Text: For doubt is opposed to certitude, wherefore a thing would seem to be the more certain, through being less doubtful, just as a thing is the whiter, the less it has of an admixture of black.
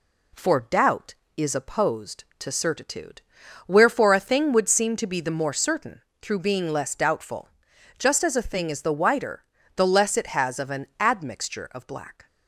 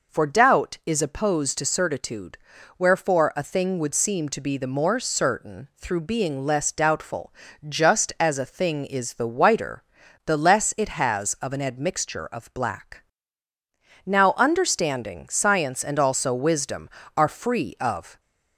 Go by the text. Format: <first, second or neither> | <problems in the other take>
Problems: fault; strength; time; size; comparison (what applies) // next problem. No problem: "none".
first | goes on to say "Now understanding science and also wisdom are free of"; strong; from 14.0 s on; 4.1 s long